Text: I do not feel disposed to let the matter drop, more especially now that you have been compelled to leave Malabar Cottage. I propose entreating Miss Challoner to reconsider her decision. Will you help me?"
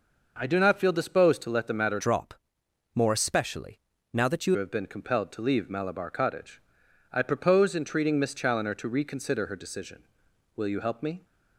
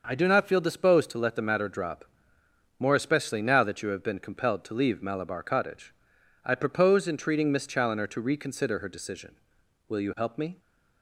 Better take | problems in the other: second | changes voice from "drop" to "you"; from 1.9 to 4.5 s; 2.6 s long // pauses between "especially" and "now"; slight; at 3.8 s; 0.32 s long

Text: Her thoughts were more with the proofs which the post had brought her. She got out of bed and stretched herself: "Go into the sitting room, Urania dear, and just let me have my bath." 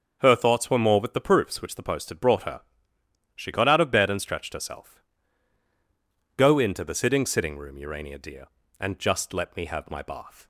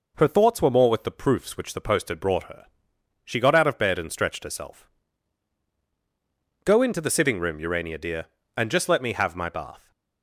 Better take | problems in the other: second | starts louder than the rest; until 1.2 s; 6 dB // says "sitting" twice; at 7.2 s

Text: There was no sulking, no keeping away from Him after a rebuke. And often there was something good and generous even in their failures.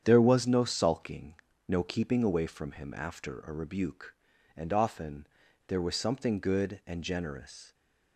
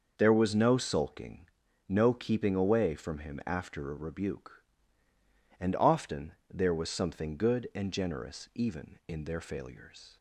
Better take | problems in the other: second | starts louder than the rest; strong; until 1.0 s; 8.5 dB; noticeable in the second // pauses between "often" and "there"; at 5.2 s; 0.42 s long; slight in the second // stops before "even in their failures"; at 7.7 s

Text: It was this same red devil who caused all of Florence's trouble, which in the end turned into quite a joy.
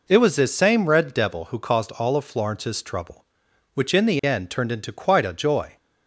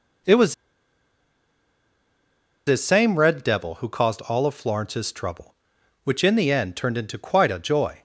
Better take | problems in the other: first | pauses between "was" and "this"; strong; at 0.5 s; 2.1 s long

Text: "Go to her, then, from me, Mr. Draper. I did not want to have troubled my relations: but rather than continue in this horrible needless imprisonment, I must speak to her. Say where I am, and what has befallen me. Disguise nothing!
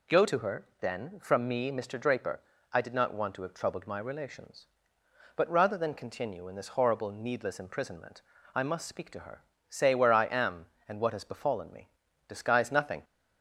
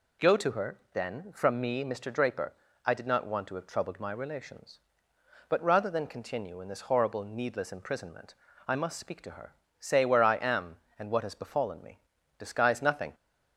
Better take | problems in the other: neither | none

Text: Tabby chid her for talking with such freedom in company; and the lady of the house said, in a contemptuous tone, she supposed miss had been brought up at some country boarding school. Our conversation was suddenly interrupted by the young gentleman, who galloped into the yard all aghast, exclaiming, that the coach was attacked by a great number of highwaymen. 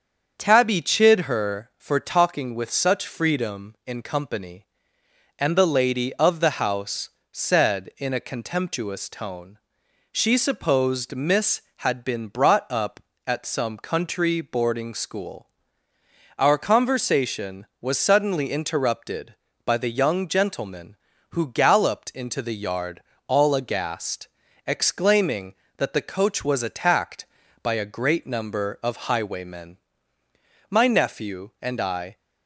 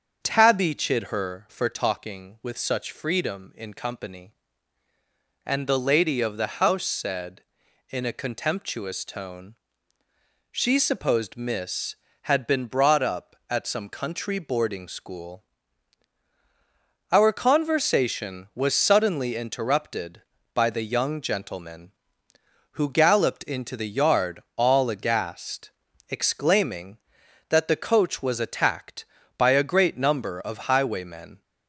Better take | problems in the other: second | starts louder than the rest; until 1.3 s; 7 dB; also in the second // pauses between "house" and "said"; slight; at 7.0 s; 0.24 s long // pauses between "yard" and "all"; slight; at 23.0 s; 0.26 s long; slight in the second // goes on to say "My nephew and I"; from 30.7 s on; 1.4 s long

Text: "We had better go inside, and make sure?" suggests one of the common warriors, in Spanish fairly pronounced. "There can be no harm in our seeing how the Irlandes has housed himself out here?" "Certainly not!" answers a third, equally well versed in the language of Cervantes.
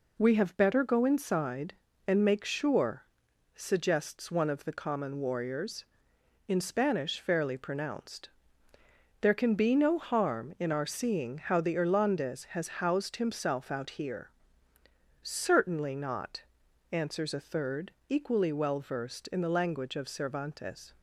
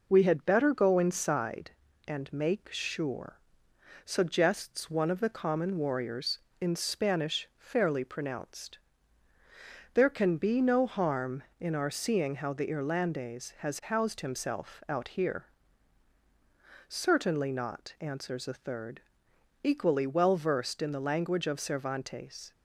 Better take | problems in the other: second | says "have" for "had"; at 0.3 s

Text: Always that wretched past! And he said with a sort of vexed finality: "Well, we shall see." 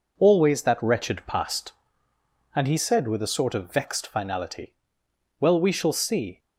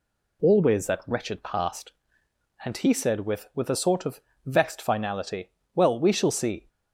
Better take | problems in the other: first | says "with" twice; at 3.5 s // pauses between "of" and "vexed"; slight; at 4.2 s; 0.26 s long

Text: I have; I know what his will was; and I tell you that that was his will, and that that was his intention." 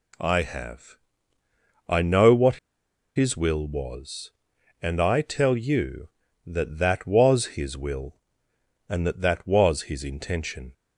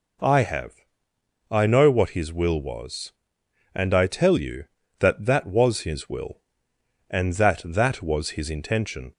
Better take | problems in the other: second | pauses between "what" and "his"; noticeable; at 2.5 s; 0.59 s long

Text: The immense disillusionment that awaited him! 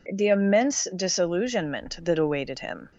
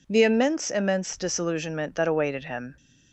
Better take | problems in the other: first | says "immense" twice; at 0.7 s

